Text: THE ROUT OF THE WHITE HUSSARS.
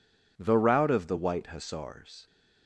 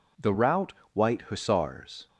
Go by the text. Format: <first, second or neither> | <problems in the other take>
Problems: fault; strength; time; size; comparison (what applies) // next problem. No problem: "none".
first | skips "OF THE"; at 0.8 s